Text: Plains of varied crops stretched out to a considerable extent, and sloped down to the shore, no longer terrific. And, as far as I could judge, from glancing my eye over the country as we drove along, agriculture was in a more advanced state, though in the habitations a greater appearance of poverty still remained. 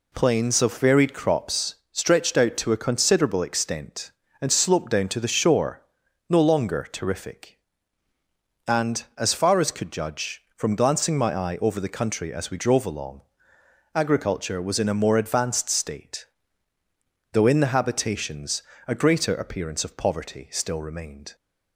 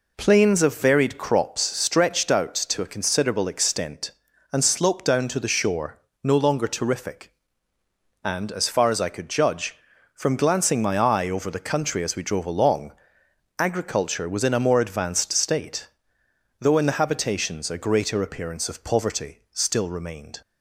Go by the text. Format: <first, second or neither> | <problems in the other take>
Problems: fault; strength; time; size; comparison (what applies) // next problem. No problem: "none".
second | pauses between "crops" and "stretched"; slight; at 1.7 s; 0.16 s long // skips "I"; at 9.7 s // pauses between "habitations" and "a"; slight; at 18.6 s; 0.24 s long